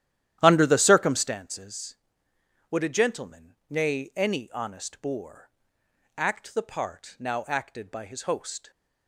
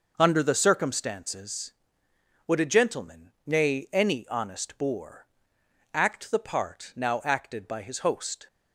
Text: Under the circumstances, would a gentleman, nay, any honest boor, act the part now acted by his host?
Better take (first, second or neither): second